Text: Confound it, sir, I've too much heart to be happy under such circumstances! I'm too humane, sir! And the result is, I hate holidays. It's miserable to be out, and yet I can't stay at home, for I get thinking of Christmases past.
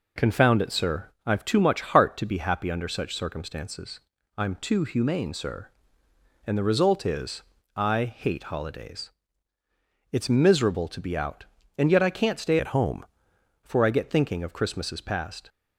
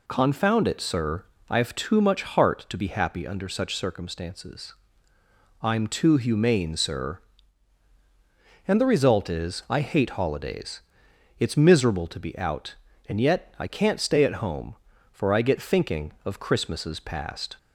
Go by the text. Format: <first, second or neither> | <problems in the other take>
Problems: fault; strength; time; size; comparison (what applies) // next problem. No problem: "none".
second | changes voice from "at" to "home"; from 12.5 to 13.0 s; 0.5 s long